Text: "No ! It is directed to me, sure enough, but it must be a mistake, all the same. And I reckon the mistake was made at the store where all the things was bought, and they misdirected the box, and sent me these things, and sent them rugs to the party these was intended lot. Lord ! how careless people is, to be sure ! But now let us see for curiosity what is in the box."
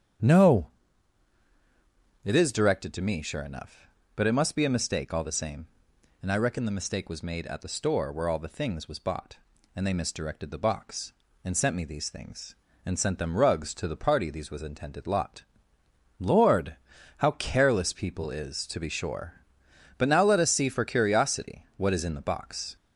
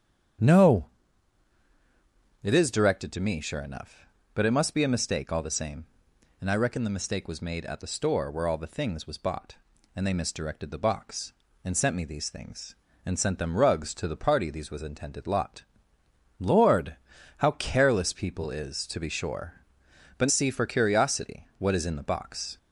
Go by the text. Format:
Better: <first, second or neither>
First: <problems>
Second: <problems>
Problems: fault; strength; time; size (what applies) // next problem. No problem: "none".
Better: first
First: starts louder than the rest; strong; until 2.7 s; 9 dB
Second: starts louder than the rest; strong; until 2.9 s; 9 dB // skips "now let us"; at 20.3 s